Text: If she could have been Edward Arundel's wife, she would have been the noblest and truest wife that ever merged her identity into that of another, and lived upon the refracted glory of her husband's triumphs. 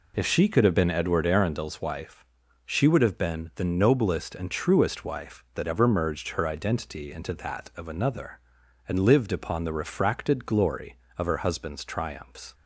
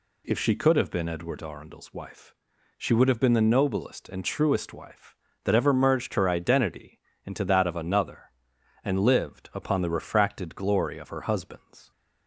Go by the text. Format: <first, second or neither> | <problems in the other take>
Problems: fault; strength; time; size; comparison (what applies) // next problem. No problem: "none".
first | pauses between "identity" and "into"; slight; at 6.9 s; 0.28 s long // stops before "triumphs"; at 11.9 s